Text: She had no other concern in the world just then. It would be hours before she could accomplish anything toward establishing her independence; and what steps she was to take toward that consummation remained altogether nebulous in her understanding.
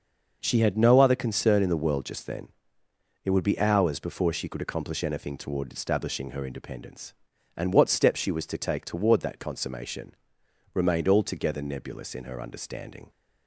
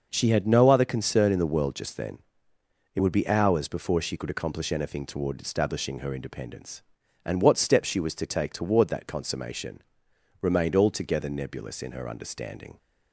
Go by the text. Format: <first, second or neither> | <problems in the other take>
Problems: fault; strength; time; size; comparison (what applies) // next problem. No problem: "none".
neither | starts louder than the rest; noticeable; the same in both // pauses between "consummation" and "remained"; noticeable; the same in both